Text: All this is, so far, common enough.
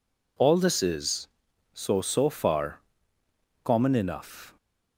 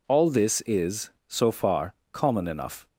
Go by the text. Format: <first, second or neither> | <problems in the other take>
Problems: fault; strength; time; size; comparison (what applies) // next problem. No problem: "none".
second | says "so" twice; at 2.0 s